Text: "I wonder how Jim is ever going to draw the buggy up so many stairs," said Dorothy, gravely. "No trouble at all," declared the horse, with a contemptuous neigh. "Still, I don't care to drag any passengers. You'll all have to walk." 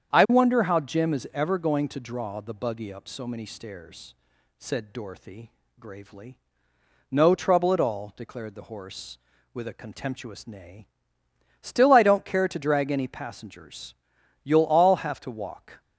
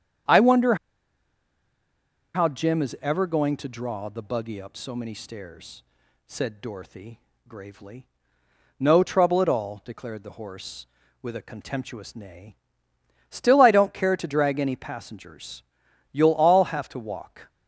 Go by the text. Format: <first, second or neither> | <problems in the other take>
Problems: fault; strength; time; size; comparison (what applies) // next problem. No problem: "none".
first | starts louder than the rest; strong; until 2.8 s; 8 dB; strong in the first // pauses between "wonder" and "how"; strong; at 0.7 s; 1.5 s long